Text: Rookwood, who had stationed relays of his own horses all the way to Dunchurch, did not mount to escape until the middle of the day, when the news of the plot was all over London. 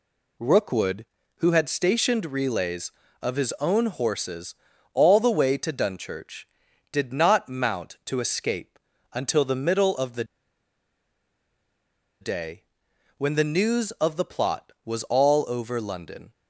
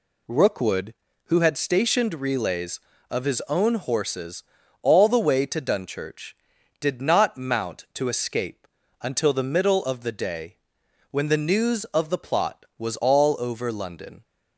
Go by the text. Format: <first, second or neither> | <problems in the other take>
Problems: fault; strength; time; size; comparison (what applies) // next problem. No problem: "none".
second | pauses between "horses" and "all"; at 4.5 s; 0.40 s long; also in the second // pauses between "escape" and "until"; slight; at 8.7 s; 0.34 s long; slight in the second // pauses between "the" and "day"; strong; at 10.2 s; 1.9 s long